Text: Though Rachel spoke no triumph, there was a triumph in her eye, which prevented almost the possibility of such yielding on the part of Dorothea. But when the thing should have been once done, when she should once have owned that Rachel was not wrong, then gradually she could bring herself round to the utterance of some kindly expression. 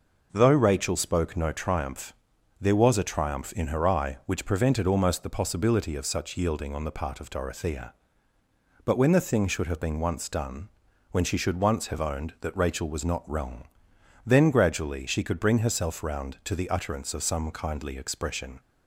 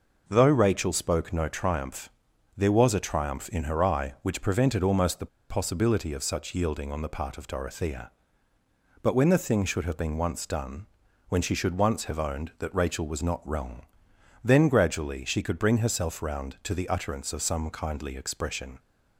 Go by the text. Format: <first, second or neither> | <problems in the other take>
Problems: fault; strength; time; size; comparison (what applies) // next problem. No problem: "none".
first | pauses between "the" and "possibility"; slight; at 5.2 s; 0.24 s long